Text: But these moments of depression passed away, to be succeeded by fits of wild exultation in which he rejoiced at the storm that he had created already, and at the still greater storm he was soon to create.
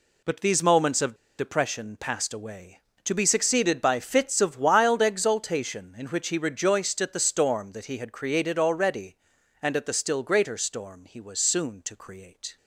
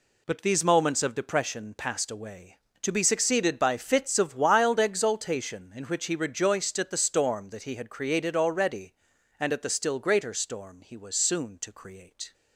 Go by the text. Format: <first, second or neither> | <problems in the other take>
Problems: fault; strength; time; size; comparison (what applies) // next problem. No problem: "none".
second | pauses between "of" and "depression"; slight; at 1.1 s; 0.22 s long